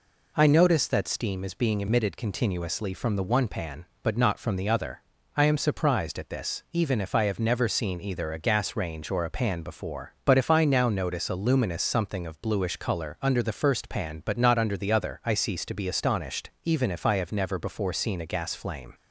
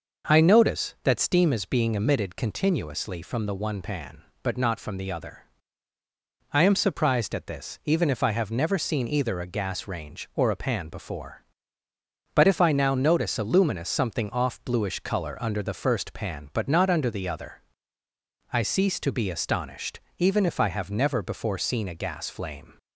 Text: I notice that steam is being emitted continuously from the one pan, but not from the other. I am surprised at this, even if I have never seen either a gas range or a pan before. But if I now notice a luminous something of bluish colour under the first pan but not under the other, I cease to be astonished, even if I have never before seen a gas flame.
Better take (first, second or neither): first